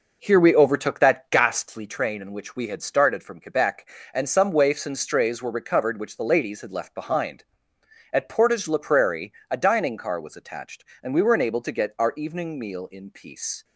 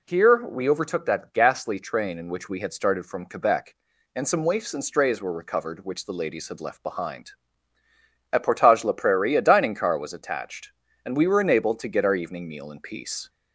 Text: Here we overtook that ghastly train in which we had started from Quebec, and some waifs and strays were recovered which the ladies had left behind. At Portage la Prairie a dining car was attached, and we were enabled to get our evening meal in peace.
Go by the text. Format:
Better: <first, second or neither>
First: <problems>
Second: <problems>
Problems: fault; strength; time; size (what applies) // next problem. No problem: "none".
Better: second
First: starts louder than the rest; noticeable; until 1.9 s; 5 dB // pauses between "Prairie" and "a"; slight; at 9.3 s; 0.18 s long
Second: none